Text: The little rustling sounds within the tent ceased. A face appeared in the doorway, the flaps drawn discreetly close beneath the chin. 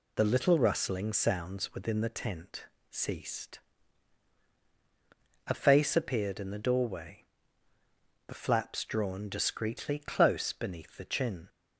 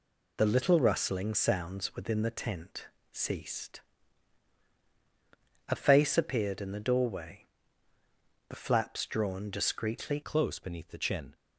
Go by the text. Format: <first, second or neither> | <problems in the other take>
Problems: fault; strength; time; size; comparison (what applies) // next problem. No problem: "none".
first | pauses between "tent" and "ceased"; slight; at 2.8 s; 0.24 s long; slight in the first // changes voice at "close"; from 10.2 s on; 1.1 s long